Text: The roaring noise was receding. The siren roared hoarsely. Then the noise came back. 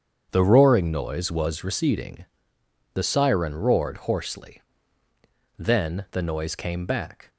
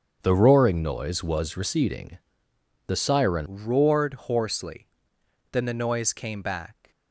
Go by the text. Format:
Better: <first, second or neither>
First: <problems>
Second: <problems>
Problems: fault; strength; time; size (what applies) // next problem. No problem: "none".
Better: first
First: starts louder than the rest; strong; until 1.3 s; 7.5 dB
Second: starts louder than the rest; until 1.2 s; 6.5 dB // changes voice at "roared"; from 3.4 s on; 3.5 s long